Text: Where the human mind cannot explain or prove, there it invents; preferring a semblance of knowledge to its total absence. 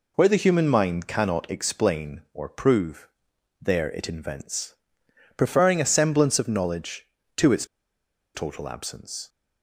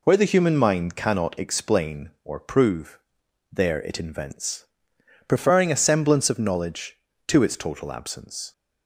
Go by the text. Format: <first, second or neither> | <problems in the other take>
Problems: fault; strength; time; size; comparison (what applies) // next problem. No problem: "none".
second | pauses between "its" and "total"; noticeable; at 7.6 s; 0.69 s long